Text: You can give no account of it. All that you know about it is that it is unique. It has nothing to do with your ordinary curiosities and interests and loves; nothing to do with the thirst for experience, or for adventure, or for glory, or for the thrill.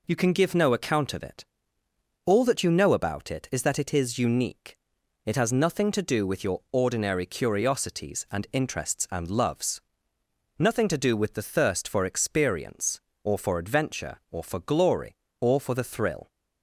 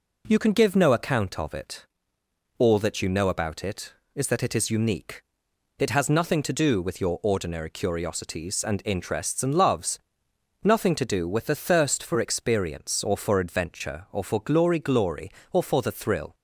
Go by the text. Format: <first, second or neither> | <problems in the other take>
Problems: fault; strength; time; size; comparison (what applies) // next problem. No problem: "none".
first | says "glory" twice; at 14.7 s